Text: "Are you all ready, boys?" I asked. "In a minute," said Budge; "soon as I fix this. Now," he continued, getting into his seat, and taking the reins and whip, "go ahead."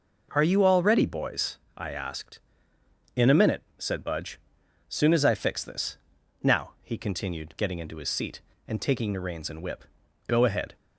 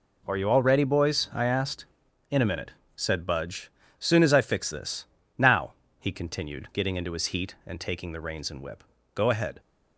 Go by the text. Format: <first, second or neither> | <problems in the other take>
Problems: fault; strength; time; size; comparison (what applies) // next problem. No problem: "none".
first | says "heat" for "seat"; at 7.2 s